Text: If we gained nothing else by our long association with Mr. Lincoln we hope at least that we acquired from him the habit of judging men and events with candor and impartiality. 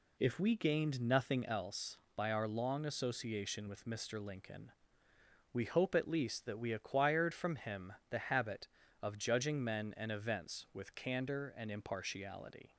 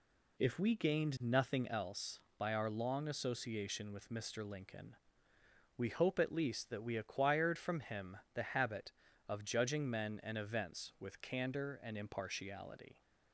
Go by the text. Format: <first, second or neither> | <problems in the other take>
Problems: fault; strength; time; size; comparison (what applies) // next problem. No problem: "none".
neither | pauses between "Lincoln" and "we"; noticeable; the same in both // pauses between "him" and "the"; slight; the same in both